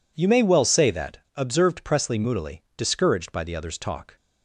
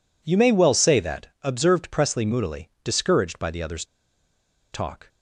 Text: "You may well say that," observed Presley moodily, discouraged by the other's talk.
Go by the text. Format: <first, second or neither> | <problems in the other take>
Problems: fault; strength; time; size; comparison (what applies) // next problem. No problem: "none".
first | pauses between "other's" and "talk"; noticeable; at 3.8 s; 0.87 s long